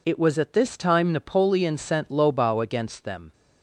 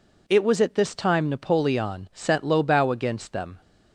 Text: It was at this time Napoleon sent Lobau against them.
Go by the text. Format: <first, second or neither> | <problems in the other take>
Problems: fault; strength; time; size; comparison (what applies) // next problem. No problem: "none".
neither | none